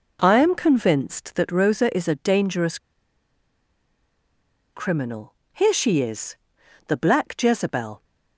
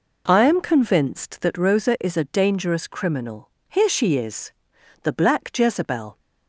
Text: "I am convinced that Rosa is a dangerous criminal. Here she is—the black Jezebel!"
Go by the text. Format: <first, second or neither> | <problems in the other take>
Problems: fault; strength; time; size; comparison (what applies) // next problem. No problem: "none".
second | pauses between "dangerous" and "criminal"; strong; at 2.7 s; 1.9 s long